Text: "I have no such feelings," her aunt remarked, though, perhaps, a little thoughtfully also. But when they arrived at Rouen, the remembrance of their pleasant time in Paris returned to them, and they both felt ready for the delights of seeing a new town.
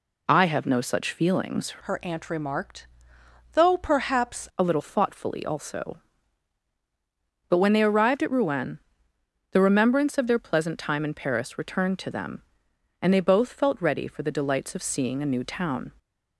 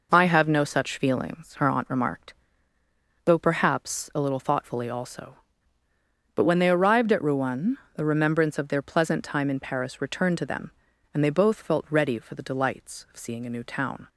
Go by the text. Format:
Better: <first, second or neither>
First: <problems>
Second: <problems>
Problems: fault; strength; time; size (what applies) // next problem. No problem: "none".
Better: second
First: changes voice from "her" to "perhaps"; from 1.7 to 4.4 s; 2.7 s long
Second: none